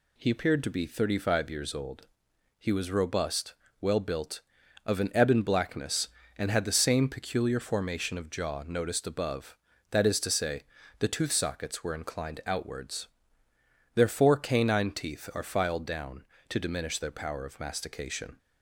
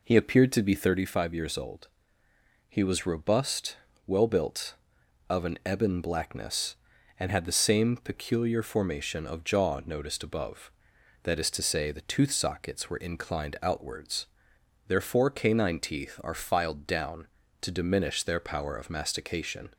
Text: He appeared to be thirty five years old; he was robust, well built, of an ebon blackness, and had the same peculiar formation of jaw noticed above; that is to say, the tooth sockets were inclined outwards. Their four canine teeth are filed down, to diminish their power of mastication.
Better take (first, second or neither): first